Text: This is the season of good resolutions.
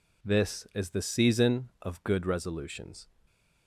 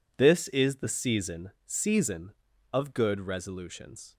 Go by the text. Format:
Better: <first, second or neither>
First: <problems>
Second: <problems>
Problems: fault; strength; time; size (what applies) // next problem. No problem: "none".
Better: first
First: none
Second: says "season" twice; at 1.6 s